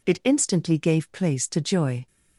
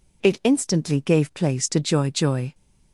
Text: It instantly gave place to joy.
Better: first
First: none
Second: says "joy" twice; at 2.1 s

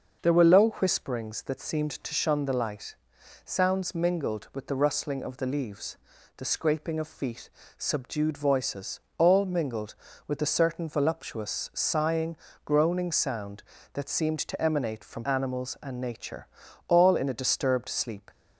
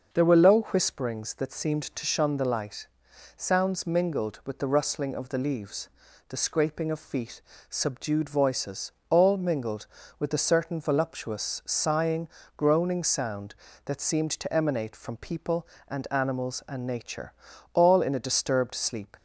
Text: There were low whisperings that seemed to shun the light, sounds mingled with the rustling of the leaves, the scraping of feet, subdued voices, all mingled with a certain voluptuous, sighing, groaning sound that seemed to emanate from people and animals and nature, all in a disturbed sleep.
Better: second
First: starts louder than the rest; noticeable; until 1.3 s; 6 dB // skips "people and"; at 15.2 s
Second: starts louder than the rest; noticeable; until 1.2 s; 6 dB

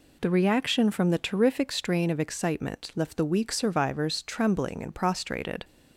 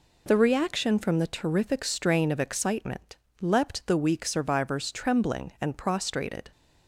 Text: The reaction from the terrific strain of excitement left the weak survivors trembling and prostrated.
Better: first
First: none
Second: says "leapt" for "left"; at 3.4 s

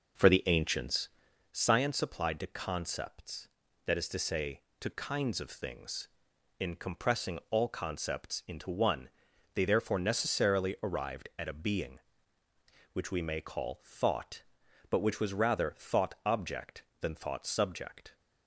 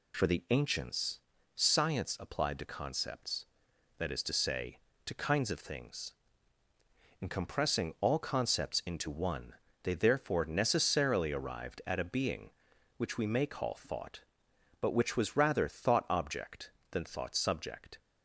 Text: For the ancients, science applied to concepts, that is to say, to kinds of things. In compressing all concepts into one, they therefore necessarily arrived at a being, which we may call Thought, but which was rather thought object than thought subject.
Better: second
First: starts louder than the rest; noticeable; until 1.5 s; 5.5 dB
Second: none

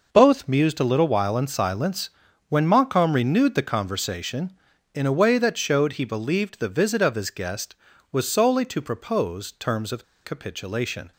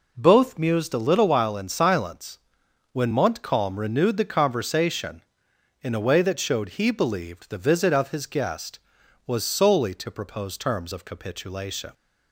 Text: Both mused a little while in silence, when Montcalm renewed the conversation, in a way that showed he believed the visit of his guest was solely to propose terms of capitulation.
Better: second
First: pauses between "of" and "capitulation"; slight; at 10.0 s; 0.20 s long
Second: none

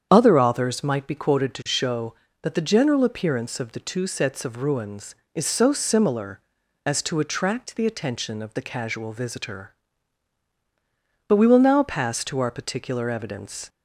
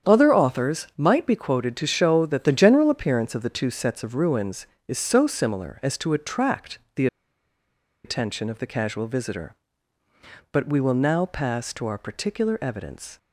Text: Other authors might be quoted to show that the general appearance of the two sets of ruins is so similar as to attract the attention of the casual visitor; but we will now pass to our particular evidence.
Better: first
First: starts louder than the rest; strong; until 1.1 s; 8 dB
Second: starts louder than the rest; strong; until 1.1 s; 8.5 dB // pauses between "attract" and "the"; slight; at 6.7 s; 0.18 s long // pauses between "the" and "attention"; noticeable; at 7.0 s; 0.98 s long

